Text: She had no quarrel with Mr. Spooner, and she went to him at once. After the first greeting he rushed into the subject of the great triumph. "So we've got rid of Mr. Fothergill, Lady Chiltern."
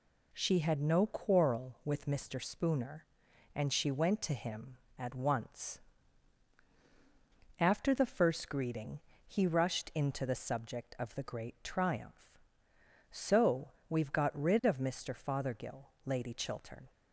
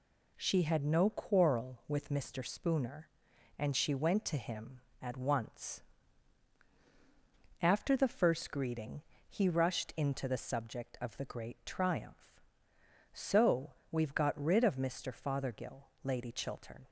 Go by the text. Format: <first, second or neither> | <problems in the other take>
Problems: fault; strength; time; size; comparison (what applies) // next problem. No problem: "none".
neither | pauses between "greeting" and "he"; slight; the same in both // pauses between "So" and "we've"; slight; the same in both